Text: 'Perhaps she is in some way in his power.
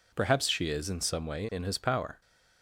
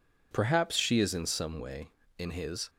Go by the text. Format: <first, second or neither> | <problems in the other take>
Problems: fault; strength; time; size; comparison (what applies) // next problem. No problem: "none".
first | stops before "power"; at 2.6 s